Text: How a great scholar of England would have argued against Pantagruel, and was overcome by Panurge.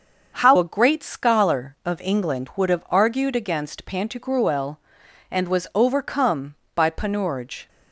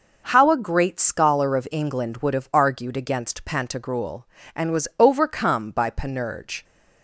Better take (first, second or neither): second